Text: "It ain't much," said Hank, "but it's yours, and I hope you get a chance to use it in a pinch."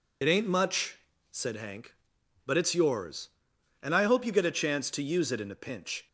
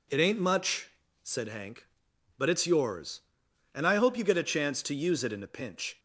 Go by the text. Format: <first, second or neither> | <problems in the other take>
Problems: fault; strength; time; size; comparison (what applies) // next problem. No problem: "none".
second | loses the start of "It"; at 0.2 s; 45 ms